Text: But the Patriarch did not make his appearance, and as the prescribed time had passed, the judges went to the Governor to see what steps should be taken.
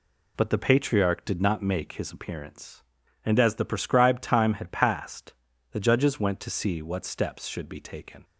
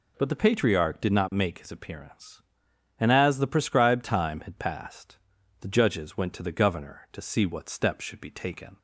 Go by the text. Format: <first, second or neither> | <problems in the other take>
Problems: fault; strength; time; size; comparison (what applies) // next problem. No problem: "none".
second | skips "the Governor to"; at 6.5 s